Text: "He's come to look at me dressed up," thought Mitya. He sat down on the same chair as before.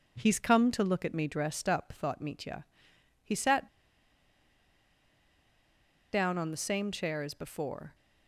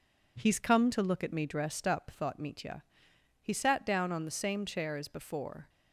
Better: second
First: pauses between "sat" and "down"; strong; at 3.6 s; 2.4 s long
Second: none

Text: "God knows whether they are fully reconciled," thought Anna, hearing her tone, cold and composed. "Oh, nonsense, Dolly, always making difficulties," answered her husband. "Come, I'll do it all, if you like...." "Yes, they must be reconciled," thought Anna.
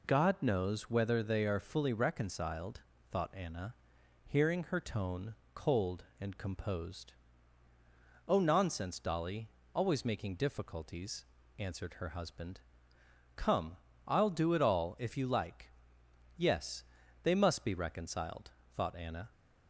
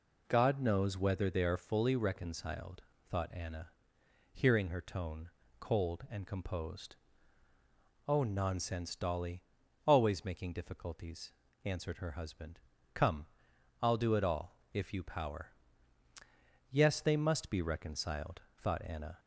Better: first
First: none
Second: says "power" for "like"; at 15.0 s

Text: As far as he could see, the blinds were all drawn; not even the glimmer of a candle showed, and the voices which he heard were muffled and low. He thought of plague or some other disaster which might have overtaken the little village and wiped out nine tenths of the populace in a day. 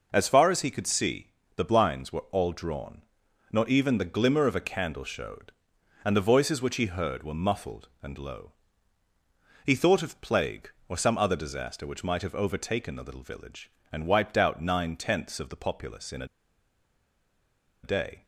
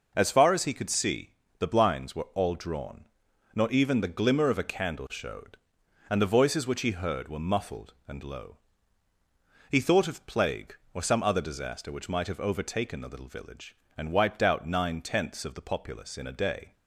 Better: second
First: pauses between "a" and "day"; strong; at 16.2 s; 1.5 s long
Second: none

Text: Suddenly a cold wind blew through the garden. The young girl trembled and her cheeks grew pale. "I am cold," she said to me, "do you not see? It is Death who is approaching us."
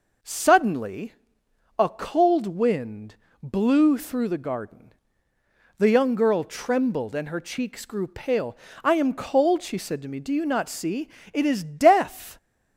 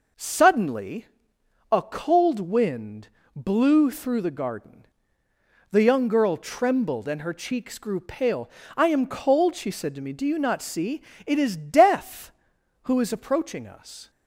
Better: second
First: pauses between "Suddenly" and "a"; noticeable; at 1.1 s; 0.66 s long // pauses between "wind" and "blew"; slight; at 3.1 s; 0.28 s long // stops before "who is approaching us"; at 12.3 s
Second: pauses between "Suddenly" and "a"; noticeable; at 1.0 s; 0.66 s long // pauses between "wind" and "blew"; slight; at 3.0 s; 0.28 s long

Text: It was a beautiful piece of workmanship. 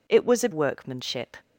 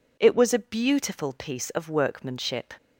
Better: second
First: skips "beautiful piece of"; at 0.5 s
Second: none

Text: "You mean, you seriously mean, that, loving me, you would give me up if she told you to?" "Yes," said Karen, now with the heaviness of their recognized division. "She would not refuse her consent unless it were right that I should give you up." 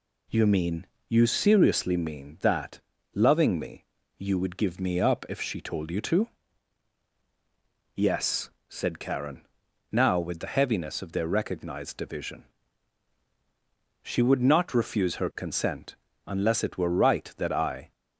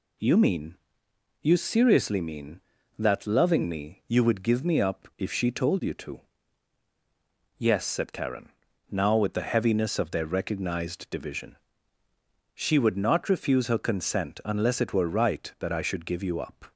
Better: second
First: pauses between "consent" and "unless"; slight; at 15.9 s; 0.30 s long // stops before "should give you up"; at 17.9 s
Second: none

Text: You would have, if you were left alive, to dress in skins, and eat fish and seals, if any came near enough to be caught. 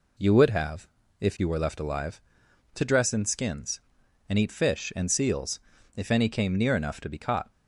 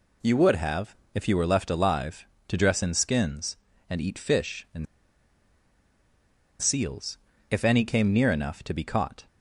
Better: first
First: none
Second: pauses between "and" and "seals"; strong; at 4.8 s; 1.7 s long

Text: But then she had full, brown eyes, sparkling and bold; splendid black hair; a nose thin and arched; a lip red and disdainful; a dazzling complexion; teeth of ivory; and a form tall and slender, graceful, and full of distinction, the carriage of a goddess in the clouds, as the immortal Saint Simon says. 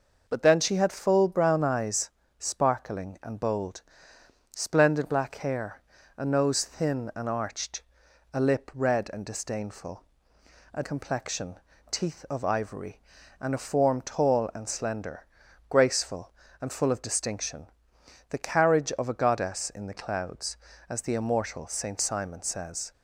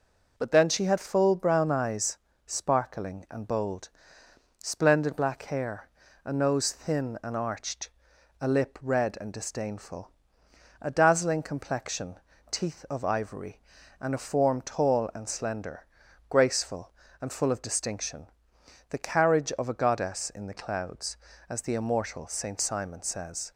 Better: second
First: skips "dazzling"; at 10.8 s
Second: none

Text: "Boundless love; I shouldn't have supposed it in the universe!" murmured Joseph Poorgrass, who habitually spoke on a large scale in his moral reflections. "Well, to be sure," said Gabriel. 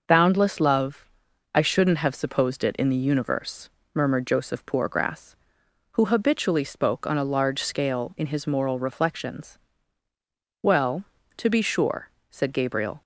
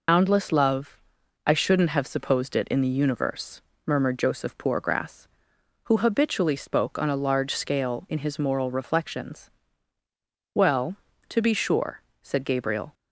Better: first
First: none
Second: loses the start of "Boundless"; at 0.0 s; 90 ms

